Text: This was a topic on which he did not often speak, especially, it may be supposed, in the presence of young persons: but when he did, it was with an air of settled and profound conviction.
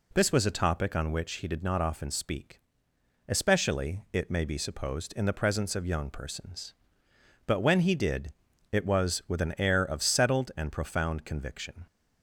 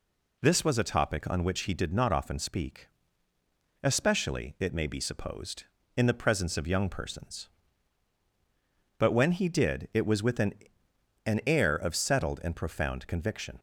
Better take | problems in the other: first | says "an" twice; at 11.2 s

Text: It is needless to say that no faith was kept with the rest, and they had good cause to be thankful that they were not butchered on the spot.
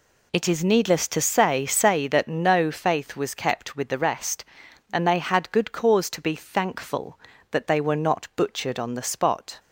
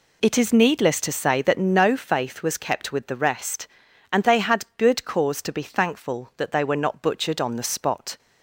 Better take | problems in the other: second | says "say" twice; at 1.6 s

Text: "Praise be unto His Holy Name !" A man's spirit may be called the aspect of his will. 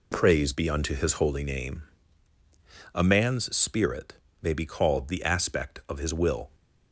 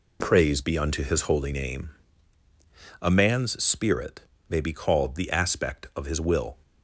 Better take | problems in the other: neither | pauses between "spirit" and "may"; slight; the same in both

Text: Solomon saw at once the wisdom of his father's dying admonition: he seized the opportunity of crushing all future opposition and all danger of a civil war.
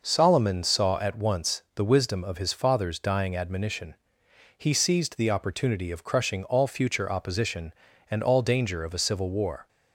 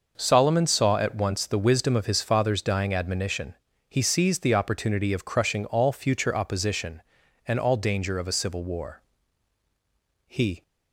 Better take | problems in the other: first | goes on to say "He"; slight; from 10.2 s on; 0.36 s long

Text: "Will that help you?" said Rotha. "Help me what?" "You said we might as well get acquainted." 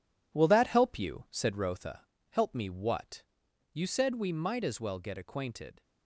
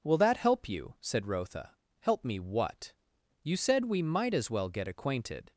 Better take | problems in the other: second | gets quieter; strong; throughout; 8.5 dB

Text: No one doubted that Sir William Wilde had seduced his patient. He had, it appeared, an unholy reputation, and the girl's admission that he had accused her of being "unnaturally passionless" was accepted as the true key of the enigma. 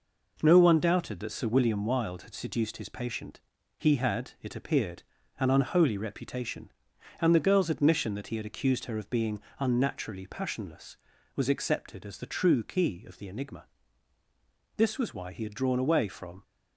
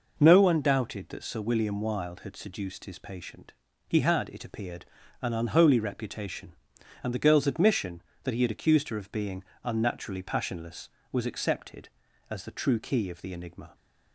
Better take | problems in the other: second | pauses between "being" and "unnaturally"; slight; at 9.3 s; 0.21 s long; slight in the second // goes on to say "This was why he had drawn away from"; strong; from 14.7 s on; 1.6 s long

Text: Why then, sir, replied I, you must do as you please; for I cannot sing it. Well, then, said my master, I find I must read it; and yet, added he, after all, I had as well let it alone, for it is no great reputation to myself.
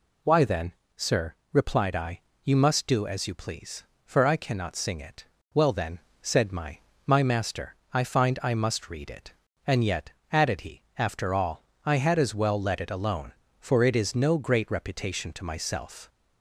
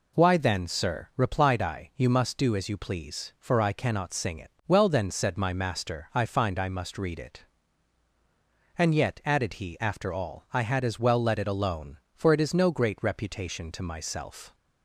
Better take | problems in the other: second | says "my" twice; at 7.0 s

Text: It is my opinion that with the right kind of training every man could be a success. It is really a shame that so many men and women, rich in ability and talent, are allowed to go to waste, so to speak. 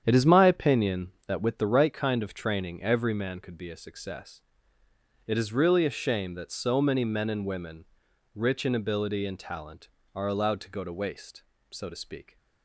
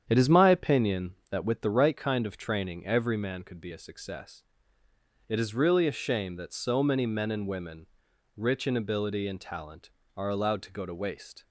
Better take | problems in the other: first | starts louder than the rest; strong; until 1.0 s; 8.5 dB; strong in the first // stops before "so to speak"; at 11.4 s

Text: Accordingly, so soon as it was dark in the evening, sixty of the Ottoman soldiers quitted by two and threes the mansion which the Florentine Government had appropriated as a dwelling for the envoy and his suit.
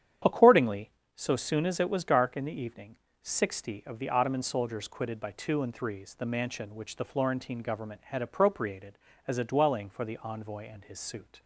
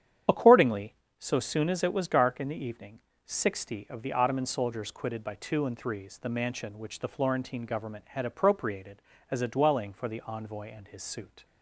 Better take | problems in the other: first | loses the start of "Accordingly"; at 0.2 s; 25 ms // starts louder than the rest; strong; until 1.5 s; 9 dB; strong in the first

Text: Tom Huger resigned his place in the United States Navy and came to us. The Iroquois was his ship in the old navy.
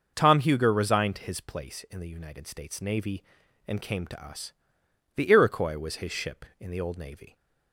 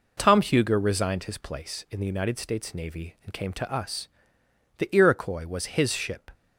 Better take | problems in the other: first | stops before "in the old navy"; at 6.3 s

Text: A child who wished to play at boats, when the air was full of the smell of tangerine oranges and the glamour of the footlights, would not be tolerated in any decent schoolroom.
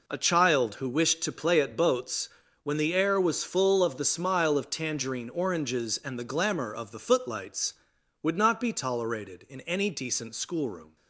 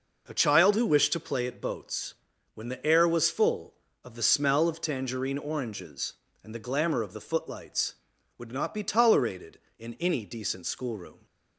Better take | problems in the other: second | says "smile" for "smell"; at 4.0 s

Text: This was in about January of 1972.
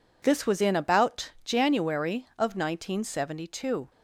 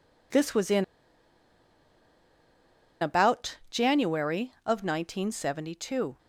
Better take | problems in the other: first | pauses between "in" and "about"; strong; at 0.8 s; 2.1 s long

